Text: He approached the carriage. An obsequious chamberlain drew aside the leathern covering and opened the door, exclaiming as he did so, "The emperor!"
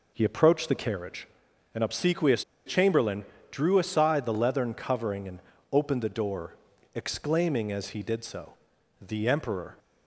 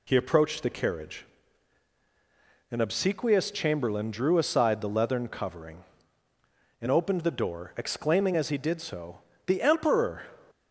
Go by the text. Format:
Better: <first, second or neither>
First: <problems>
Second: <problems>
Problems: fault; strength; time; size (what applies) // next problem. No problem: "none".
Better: second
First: pauses between "obsequious" and "chamberlain"; slight; at 2.4 s; 0.22 s long // pauses between "chamberlain" and "drew"; slight; at 3.2 s; 0.26 s long // pauses between "and" and "opened"; slight; at 5.4 s; 0.32 s long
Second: none